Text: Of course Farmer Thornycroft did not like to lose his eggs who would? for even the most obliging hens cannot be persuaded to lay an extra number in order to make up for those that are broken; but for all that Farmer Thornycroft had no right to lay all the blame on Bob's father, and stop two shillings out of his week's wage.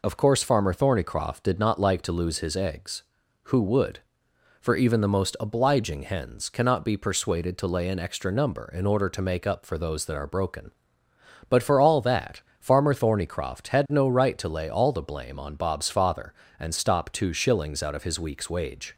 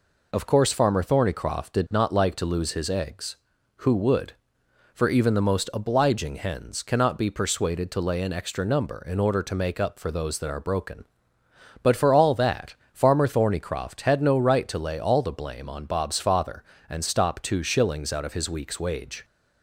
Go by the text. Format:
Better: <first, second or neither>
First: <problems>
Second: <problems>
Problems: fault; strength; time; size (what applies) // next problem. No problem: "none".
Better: neither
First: pauses between "that" and "Farmer"; slight; at 12.4 s; 0.18 s long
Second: pauses between "that" and "Farmer"; slight; at 12.7 s; 0.18 s long